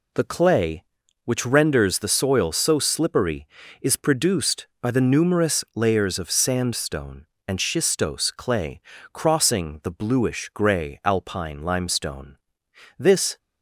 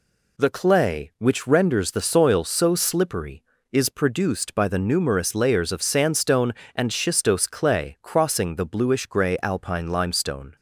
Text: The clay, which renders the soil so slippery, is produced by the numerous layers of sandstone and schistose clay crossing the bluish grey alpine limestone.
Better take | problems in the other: second | pauses between "clay" and "crossing"; slight; at 8.8 s; 0.32 s long // goes on to say "This"; slight; from 12.9 s on; 0.38 s long

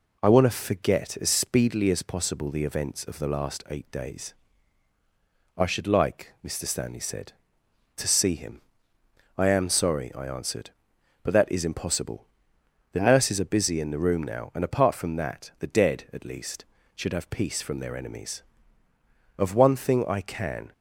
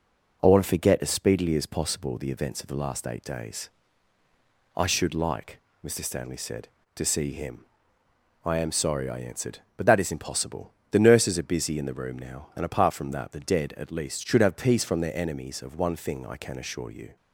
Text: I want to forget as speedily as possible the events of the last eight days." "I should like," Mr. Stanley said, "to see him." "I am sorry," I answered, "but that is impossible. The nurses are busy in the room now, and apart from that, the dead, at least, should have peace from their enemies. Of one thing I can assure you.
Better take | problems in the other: second | stops before "assure you"; at 20.7 s

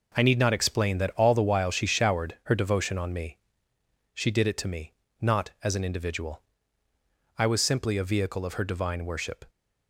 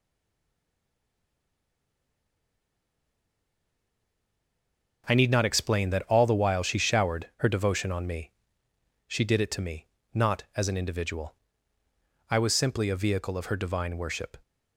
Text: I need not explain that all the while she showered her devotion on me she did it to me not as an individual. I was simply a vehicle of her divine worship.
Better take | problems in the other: first | stays silent before the first word; strong; until 5.0 s; 5.0 s long // pauses between "me" and "she"; noticeable; at 8.3 s; 0.76 s long; noticeable in the first // pauses between "me" and "not"; slight; at 9.8 s; 0.29 s long; slight in the first

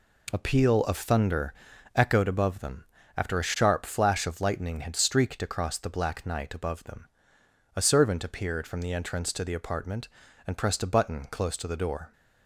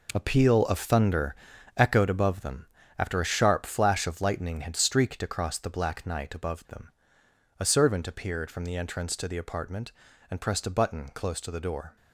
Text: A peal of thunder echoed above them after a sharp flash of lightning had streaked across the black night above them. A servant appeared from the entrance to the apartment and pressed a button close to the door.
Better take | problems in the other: first | gets quieter; strong; throughout; 9 dB // pauses between "thunder" and "echoed"; at 1.3 s; 0.40 s long; also in the first // pauses between "them" and "after"; slight; at 2.6 s; 0.32 s long; slight in the first

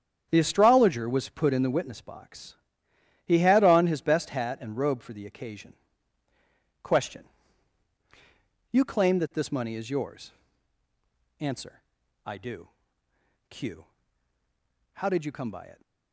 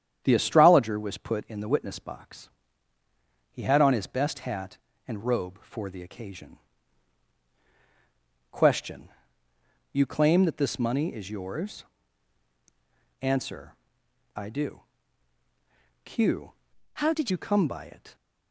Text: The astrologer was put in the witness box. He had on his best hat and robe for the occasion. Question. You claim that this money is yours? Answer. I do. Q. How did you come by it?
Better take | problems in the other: first | starts louder than the rest; strong; until 1.2 s; 9 dB; strong in the first // changes voice from "How" to "did"; from 16.9 to 17.3 s; 0.4 s long

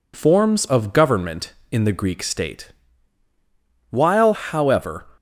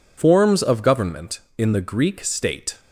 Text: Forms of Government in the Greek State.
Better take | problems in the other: second | goes on to say "While however"; noticeable; from 3.8 s on; 1.1 s long

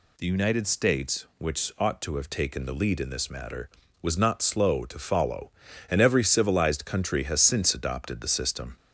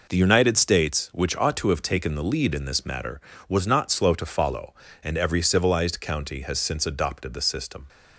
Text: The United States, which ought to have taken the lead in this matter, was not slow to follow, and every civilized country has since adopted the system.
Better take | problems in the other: first | says "county" for "country"; at 6.0 s

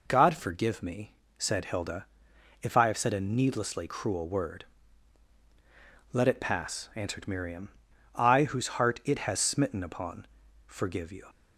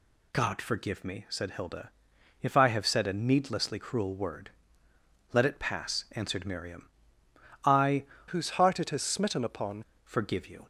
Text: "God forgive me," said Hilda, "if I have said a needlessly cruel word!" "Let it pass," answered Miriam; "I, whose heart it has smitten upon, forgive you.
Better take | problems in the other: first | changes voice from "whose" to "upon"; from 8.2 to 9.8 s; 1.6 s long

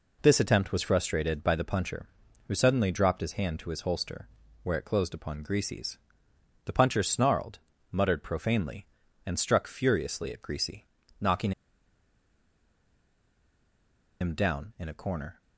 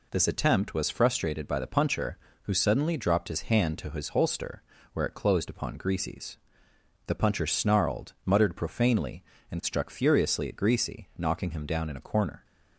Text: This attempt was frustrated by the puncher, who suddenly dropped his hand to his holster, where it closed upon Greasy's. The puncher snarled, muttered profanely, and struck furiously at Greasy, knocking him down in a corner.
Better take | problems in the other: second | pauses between "knocking" and "him"; strong; at 11.5 s; 2.6 s long

